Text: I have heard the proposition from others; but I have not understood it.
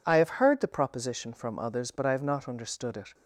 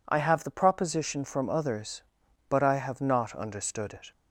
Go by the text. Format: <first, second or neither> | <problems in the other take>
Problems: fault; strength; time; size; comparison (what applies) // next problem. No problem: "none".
first | skips "heard"; at 0.4 s